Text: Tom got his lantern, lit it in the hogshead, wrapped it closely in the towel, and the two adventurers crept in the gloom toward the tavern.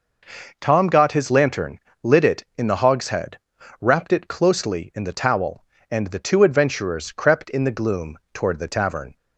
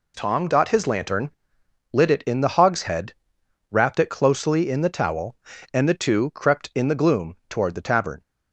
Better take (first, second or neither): first